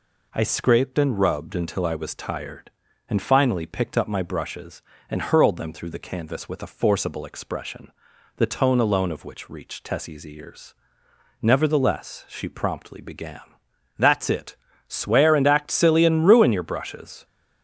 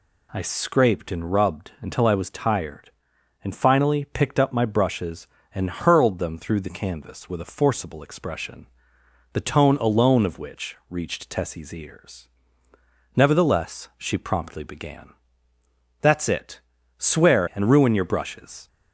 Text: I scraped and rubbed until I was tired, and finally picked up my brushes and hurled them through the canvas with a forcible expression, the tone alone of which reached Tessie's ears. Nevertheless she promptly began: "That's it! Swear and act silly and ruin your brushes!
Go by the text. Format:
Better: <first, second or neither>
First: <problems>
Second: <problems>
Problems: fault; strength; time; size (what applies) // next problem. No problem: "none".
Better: first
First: none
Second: skips "and act silly"; at 17.5 s